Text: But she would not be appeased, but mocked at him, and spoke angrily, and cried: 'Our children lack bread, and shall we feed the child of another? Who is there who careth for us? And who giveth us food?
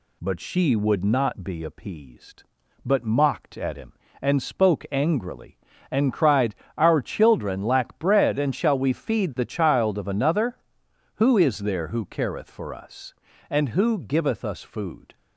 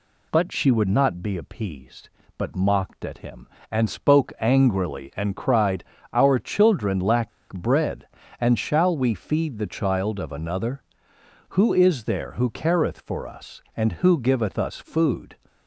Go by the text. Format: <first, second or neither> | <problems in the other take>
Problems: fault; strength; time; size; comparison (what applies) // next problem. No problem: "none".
first | pauses between "lack" and "bread"; slight; at 7.3 s; 0.22 s long